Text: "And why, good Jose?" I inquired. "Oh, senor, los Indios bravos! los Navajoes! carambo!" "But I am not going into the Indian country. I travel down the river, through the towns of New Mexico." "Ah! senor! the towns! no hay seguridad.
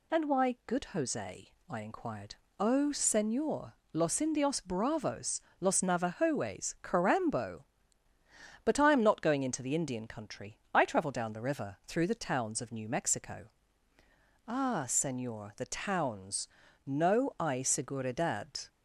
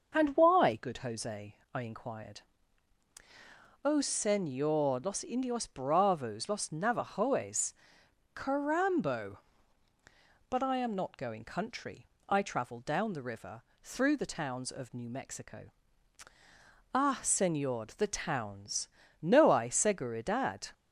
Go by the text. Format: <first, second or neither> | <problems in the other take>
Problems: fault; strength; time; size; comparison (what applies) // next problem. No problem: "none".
first | starts louder than the rest; until 1.1 s; 6 dB // skips "into the Indian"; at 11.4 s